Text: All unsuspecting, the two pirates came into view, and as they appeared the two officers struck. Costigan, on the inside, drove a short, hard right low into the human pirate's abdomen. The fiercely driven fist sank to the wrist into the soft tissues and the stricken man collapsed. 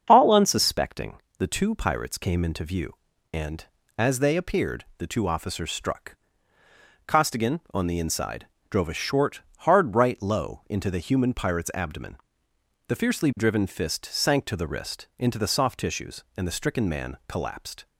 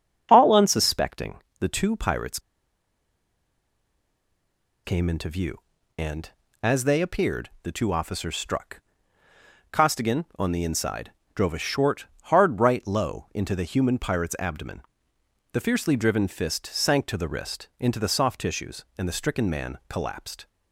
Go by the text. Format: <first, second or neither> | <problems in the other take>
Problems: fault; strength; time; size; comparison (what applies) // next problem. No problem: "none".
first | starts louder than the rest; strong; until 1.3 s; 7 dB; strong in the first // pauses between "pirates" and "came"; strong; at 2.3 s; 2.4 s long